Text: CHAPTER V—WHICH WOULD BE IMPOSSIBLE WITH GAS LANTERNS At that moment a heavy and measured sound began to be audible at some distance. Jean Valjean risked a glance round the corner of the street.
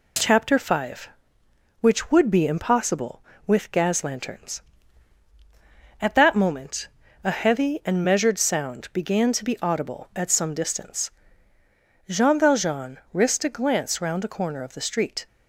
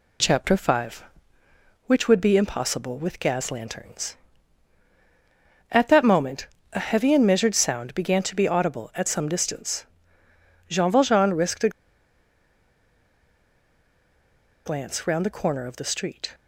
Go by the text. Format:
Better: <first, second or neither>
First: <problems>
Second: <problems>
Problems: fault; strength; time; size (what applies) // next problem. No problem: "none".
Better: first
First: pauses between "moment" and "a"; slight; at 6.8 s; 0.36 s long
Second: pauses between "moment" and "a"; slight; at 6.4 s; 0.28 s long // pauses between "a" and "glance"; strong; at 11.6 s; 2.9 s long